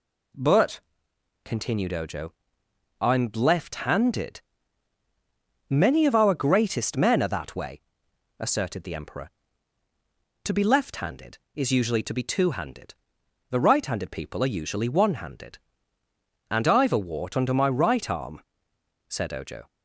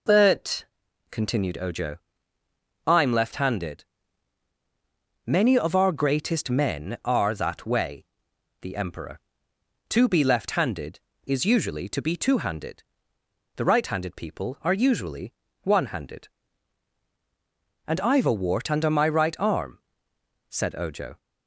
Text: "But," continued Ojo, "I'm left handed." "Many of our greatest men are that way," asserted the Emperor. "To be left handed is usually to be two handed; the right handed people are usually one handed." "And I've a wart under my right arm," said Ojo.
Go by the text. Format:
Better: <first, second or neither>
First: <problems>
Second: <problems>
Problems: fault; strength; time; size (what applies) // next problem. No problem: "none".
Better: first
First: none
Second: skips "asserted"; at 8.3 s // pauses between "usually" and "one"; slight; at 15.3 s; 0.30 s long